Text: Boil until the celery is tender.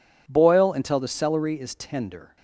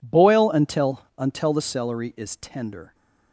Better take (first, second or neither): first